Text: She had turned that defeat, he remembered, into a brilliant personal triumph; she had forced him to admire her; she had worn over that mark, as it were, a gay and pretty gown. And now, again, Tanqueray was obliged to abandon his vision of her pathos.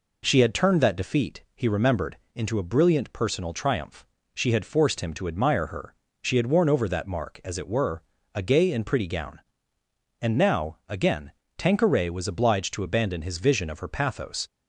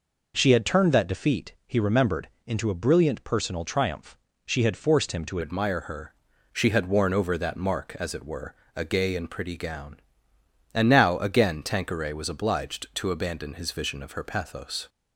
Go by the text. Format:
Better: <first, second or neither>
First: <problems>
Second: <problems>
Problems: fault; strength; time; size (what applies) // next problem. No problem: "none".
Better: first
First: none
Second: changes voice at "admire"; from 5.4 s on; 9.4 s long